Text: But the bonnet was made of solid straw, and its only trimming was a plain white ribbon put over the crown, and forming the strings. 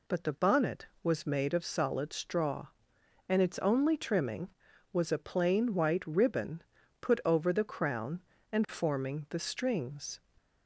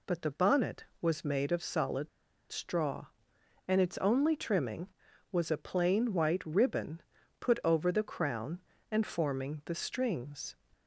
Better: first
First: pauses between "ribbon" and "put"; at 6.6 s; 0.38 s long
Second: pauses between "solid" and "straw"; at 2.0 s; 0.42 s long // pauses between "ribbon" and "put"; at 7.0 s; 0.38 s long

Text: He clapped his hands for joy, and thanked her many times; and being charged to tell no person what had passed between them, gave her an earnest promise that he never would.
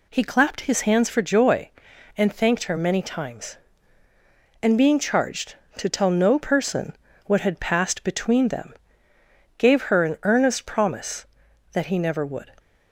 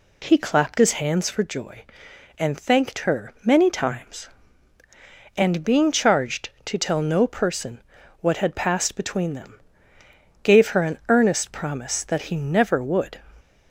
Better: neither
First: pauses between "person" and "what"; slight; at 6.9 s; 0.30 s long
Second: pauses between "person" and "what"; at 7.8 s; 0.40 s long

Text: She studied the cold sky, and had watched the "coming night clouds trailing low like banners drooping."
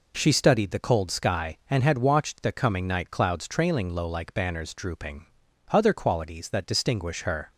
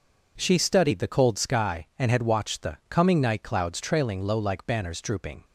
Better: second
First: goes on to say "Other qualities that distinguish her"; strong; from 5.7 s on; 1.7 s long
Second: none

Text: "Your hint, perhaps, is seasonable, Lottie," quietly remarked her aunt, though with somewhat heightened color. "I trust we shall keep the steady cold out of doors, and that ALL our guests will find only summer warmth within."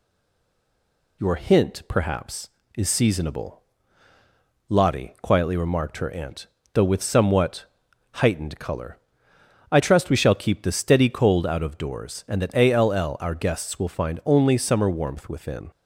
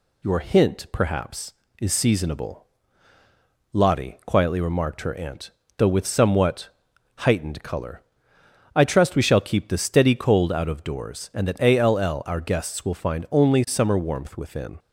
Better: second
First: stays silent before the first word; noticeable; until 1.2 s; 1.2 s long // pauses between "somewhat" and "heightened"; noticeable; at 7.6 s; 0.48 s long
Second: pauses between "somewhat" and "heightened"; noticeable; at 6.7 s; 0.48 s long

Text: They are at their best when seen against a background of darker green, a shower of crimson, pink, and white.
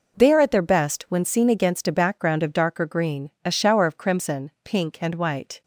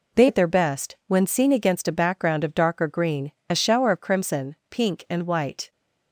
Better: first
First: none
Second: skips "are"; at 0.2 s

